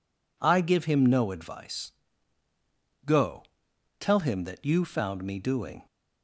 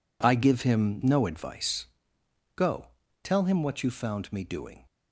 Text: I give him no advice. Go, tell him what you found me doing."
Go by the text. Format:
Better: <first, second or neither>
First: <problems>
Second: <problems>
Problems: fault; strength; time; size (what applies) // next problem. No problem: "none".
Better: second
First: says "that" for "what"; at 4.4 s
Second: none